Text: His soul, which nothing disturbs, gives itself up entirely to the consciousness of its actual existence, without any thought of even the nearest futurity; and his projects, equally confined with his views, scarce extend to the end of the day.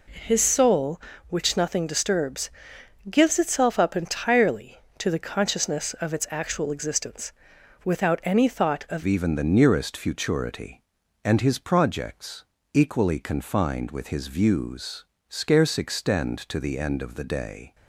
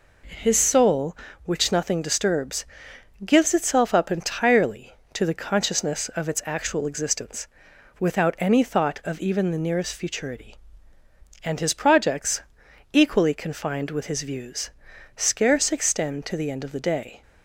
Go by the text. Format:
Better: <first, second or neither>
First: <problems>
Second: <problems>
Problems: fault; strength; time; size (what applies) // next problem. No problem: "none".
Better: second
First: changes voice at "even"; from 9.0 s on; 8.7 s long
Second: none